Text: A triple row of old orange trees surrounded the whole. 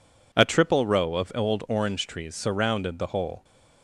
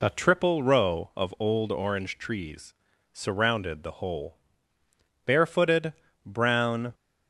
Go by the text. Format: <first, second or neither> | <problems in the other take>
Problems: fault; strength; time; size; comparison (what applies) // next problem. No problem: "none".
first | pauses between "trees" and "surrounded"; at 2.7 s; 0.38 s long // goes on to say "Barefooted brown"; strong; from 5.2 s on; 1.6 s long